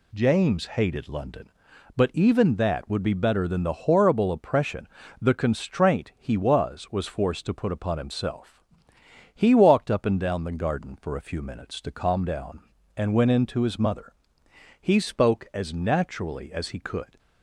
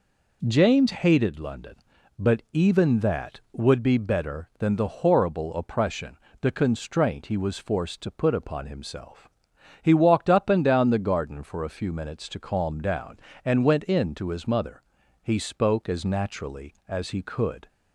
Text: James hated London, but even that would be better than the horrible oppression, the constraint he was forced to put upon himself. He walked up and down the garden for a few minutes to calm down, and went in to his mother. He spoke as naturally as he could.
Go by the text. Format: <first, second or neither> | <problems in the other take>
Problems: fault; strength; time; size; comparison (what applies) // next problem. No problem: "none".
second | says "was" twice; at 6.9 s